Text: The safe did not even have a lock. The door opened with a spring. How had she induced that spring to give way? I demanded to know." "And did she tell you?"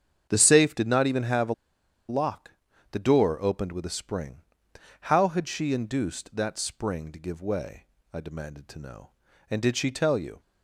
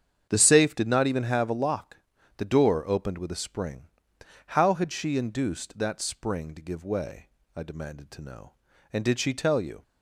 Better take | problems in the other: second | starts louder than the rest; strong; until 1.3 s; 8 dB; strong in the second // pauses between "a" and "lock"; noticeable; at 1.5 s; 0.55 s long

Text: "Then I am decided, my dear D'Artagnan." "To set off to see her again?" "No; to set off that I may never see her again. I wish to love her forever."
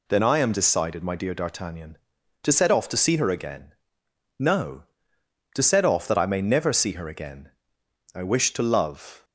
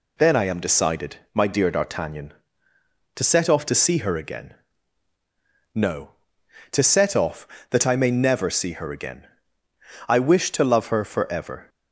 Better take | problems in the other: second | stops before "her forever"; at 9.2 s

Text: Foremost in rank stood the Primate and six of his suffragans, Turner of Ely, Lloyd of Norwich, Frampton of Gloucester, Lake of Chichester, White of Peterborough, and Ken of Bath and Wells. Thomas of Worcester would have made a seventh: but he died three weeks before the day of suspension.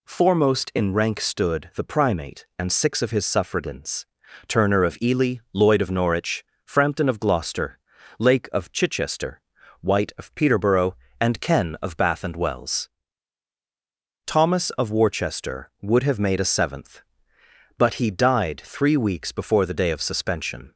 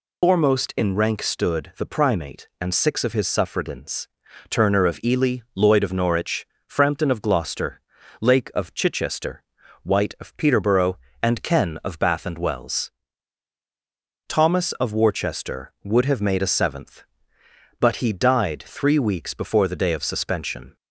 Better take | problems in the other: first | loses the start of "Foremost"; at 0.2 s; 155 ms

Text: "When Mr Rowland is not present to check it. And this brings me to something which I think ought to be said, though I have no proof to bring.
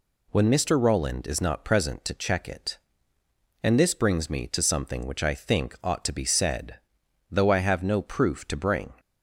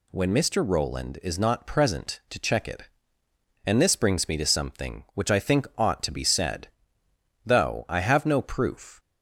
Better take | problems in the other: first | stops before "to bring"; at 8.9 s

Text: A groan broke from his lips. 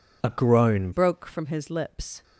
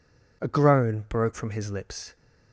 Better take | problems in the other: second | changes voice at "broke"; from 0.9 s on; 1.3 s long

